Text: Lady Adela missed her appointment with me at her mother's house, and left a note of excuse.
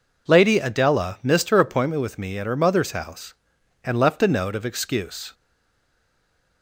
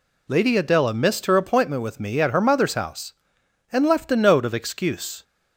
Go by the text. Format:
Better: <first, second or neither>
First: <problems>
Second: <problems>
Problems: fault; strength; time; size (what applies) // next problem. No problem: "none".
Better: second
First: stays silent after the last word; noticeable; from 5.3 s on; 1.3 s long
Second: none